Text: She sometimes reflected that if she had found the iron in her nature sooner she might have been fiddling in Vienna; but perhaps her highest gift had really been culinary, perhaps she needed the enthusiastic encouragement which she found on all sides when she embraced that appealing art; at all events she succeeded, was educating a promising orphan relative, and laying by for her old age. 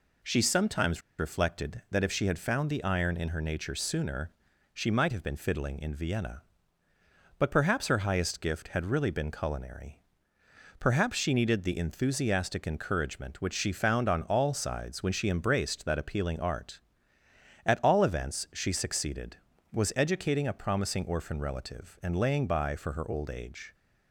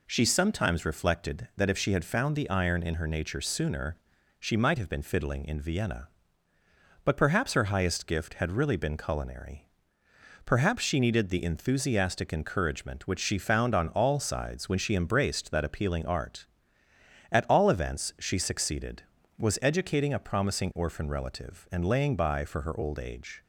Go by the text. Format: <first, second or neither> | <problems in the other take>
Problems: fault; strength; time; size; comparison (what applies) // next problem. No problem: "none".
second | pauses between "sometimes" and "reflected"; slight; at 1.0 s; 0.18 s long // pauses between "sooner" and "she"; at 4.3 s; 0.42 s long; also in the second